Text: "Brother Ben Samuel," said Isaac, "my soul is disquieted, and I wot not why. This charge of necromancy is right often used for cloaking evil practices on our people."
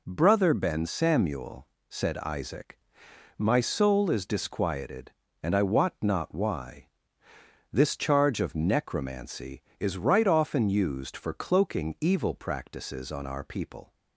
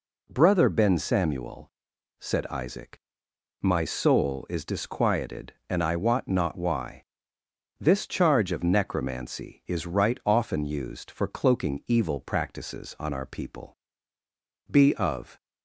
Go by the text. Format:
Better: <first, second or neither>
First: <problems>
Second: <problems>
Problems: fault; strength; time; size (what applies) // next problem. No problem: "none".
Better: first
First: none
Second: goes on to say "Be of"; noticeable; from 14.7 s on; 0.70 s long